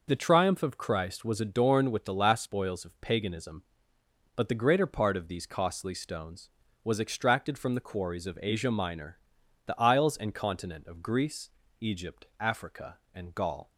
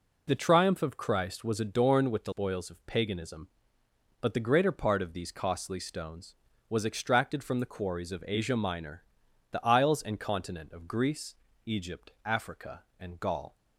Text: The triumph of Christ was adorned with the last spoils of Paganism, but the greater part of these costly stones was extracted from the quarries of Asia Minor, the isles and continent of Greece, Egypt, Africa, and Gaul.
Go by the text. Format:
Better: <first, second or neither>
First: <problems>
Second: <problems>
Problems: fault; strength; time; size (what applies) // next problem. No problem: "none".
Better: first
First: none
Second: skips "last"; at 2.3 s